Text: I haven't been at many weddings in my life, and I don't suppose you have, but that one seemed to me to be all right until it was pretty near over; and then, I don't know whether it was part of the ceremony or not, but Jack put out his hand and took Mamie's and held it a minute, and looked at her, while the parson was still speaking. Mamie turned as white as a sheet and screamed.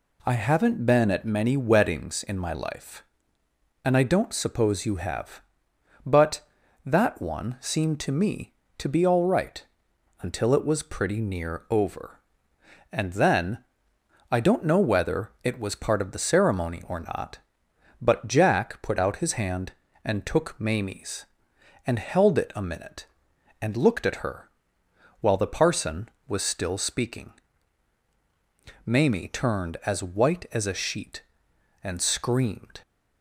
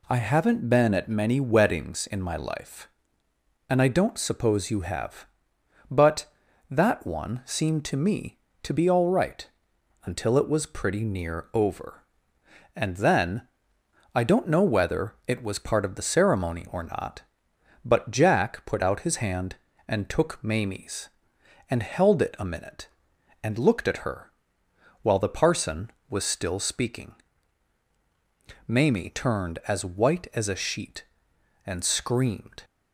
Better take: neither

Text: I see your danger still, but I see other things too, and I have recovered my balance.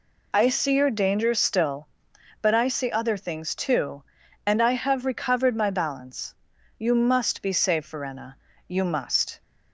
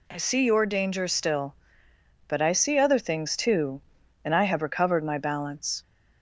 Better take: second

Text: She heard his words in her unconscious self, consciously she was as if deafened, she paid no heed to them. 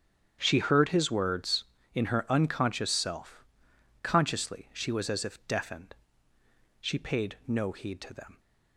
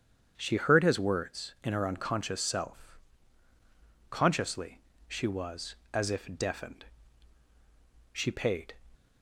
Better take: first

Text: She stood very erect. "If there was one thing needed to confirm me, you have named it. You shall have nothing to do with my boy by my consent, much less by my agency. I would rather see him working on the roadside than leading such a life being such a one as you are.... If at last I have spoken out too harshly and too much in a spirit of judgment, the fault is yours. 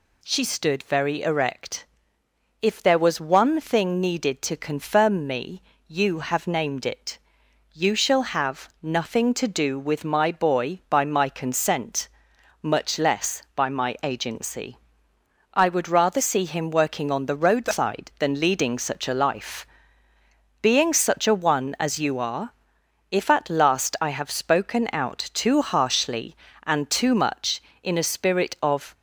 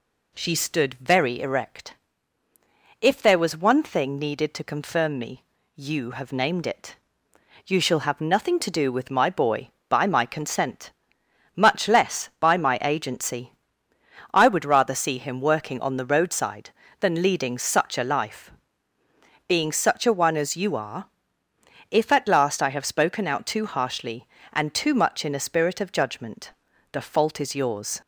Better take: second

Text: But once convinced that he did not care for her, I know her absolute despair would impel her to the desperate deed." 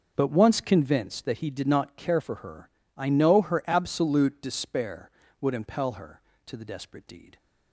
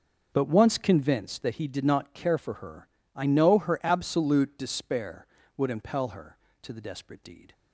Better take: neither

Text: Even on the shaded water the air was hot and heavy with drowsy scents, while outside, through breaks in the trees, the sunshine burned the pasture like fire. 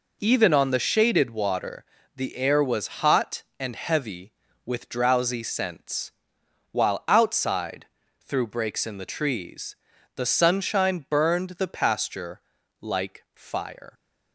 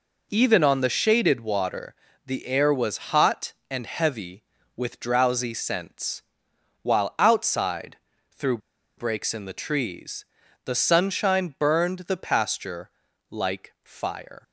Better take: first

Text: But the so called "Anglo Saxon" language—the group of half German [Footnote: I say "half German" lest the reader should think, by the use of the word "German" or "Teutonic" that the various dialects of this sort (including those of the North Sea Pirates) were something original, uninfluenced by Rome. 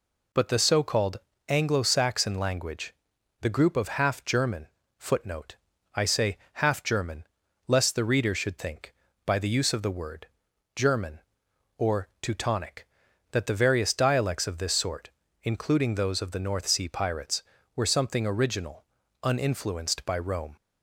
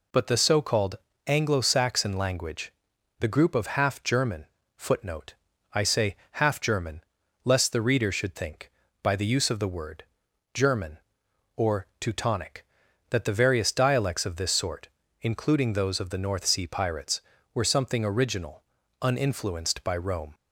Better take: neither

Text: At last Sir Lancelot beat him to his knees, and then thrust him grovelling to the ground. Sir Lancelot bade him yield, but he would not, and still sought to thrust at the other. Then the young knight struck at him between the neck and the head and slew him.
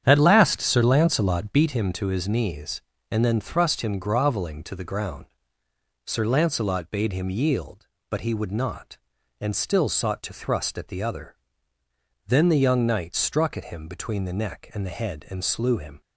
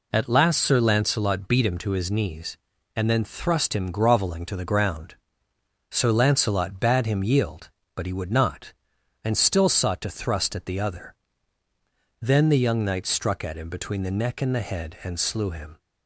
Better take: second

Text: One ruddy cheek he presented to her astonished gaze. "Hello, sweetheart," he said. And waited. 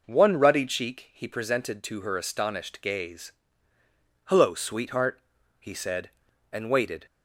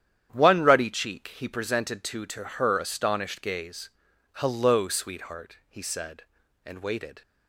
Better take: first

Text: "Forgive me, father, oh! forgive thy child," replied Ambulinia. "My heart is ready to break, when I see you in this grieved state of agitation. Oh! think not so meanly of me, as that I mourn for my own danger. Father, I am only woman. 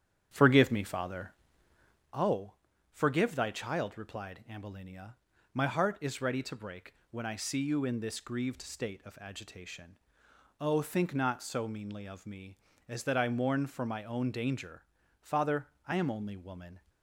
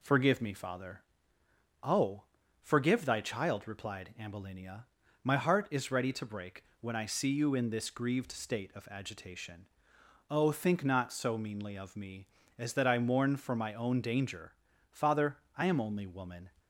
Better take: second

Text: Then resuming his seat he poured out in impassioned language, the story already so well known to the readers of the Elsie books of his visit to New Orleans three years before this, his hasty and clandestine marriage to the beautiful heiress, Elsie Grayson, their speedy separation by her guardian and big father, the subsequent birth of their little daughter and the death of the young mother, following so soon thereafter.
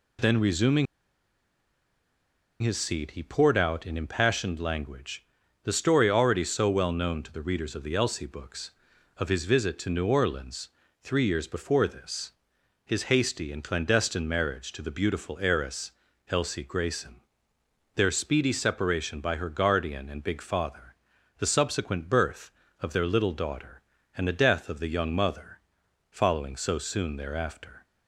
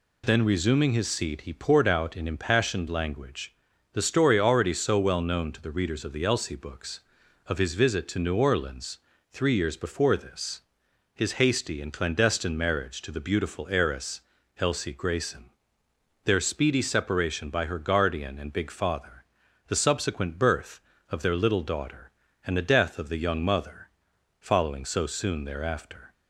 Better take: second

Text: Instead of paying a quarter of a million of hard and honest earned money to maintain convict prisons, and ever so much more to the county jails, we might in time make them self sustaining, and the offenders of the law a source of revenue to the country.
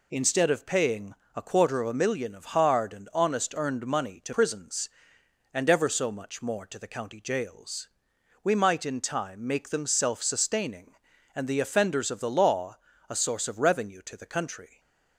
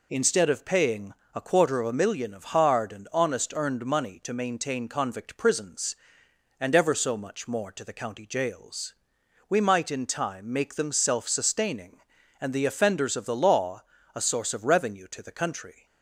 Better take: second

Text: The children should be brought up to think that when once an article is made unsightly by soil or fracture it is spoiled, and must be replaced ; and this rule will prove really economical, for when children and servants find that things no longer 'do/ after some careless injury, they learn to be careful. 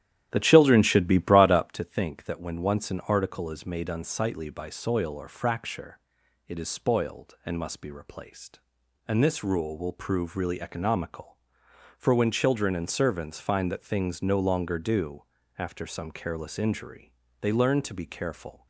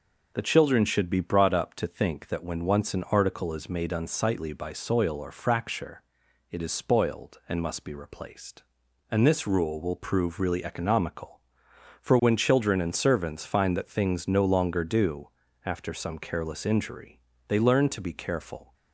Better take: second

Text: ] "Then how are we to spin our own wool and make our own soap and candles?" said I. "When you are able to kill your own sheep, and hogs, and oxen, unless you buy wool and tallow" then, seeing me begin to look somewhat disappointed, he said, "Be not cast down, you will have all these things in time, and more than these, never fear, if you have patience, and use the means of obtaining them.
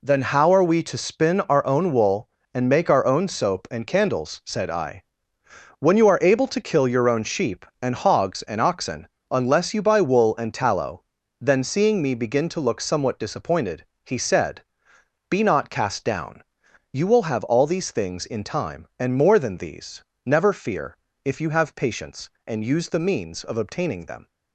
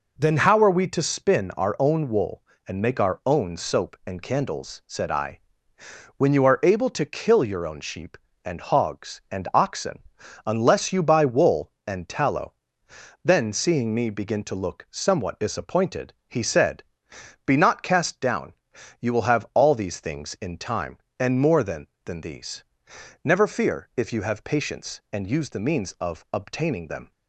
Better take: first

